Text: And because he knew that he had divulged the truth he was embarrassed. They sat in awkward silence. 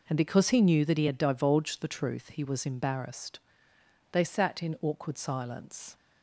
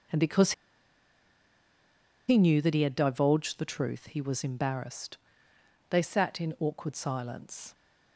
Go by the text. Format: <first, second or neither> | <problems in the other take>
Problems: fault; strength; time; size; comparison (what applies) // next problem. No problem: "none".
first | pauses between "because" and "he"; strong; at 0.5 s; 1.7 s long